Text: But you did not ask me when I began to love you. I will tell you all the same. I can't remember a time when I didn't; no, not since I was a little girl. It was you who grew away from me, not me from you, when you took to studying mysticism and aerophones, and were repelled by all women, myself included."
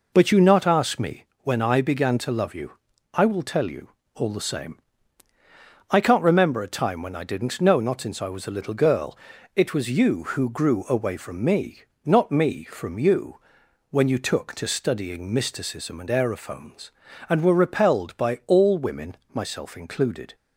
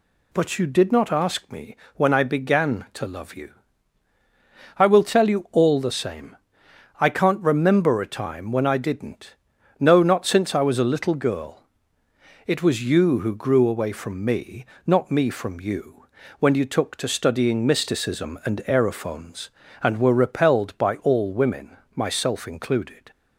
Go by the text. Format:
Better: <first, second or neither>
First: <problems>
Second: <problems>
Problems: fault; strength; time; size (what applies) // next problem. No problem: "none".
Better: second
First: skips "did"; at 0.4 s // pauses between "me" and "when"; slight; at 1.2 s; 0.18 s long // pauses between "you" and "all"; slight; at 3.8 s; 0.24 s long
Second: pauses between "me" and "when"; slight; at 1.7 s; 0.20 s long